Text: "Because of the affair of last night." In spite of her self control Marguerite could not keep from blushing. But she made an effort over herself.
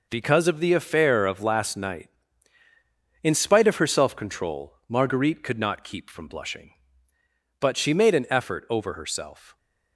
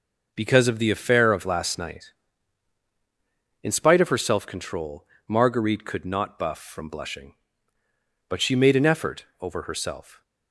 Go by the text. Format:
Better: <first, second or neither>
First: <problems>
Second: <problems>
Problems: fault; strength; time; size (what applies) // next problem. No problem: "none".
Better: first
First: none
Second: pauses between "control" and "Marguerite"; slight; at 5.0 s; 0.22 s long // says "buff" for "keep"; at 6.3 s